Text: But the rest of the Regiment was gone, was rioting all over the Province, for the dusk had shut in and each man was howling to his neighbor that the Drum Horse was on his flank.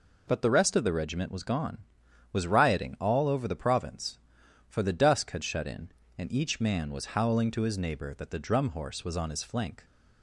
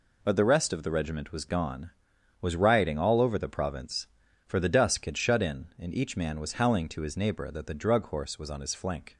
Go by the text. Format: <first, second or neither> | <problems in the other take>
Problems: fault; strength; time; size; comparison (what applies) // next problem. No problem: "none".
first | says "Drug" for "Drum"; at 7.7 s